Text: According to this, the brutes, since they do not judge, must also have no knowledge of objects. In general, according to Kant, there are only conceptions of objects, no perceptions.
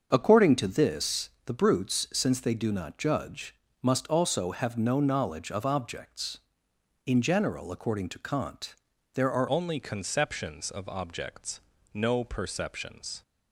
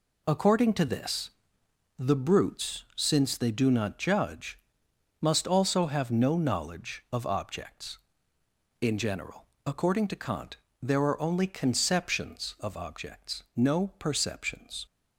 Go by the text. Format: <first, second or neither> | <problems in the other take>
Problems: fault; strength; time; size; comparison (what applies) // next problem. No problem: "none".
second | starts louder than the rest; until 1.1 s; 6.5 dB // changes voice at "only"; from 9.4 s on; 3.8 s long